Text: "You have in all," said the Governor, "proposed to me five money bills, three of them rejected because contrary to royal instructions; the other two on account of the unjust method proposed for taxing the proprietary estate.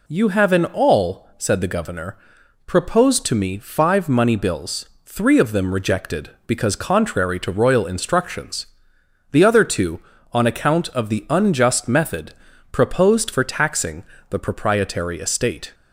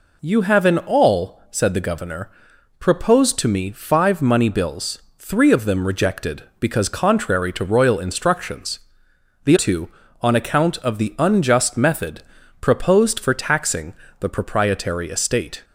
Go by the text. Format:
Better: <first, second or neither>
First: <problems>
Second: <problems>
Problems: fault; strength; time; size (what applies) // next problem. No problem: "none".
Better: first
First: pauses between "method" and "proposed"; slight; at 12.3 s; 0.36 s long // pauses between "taxing" and "the"; slight; at 14.0 s; 0.26 s long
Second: skips "other"; at 9.5 s // pauses between "method" and "proposed"; slight; at 12.2 s; 0.36 s long // pauses between "taxing" and "the"; slight; at 13.9 s; 0.26 s long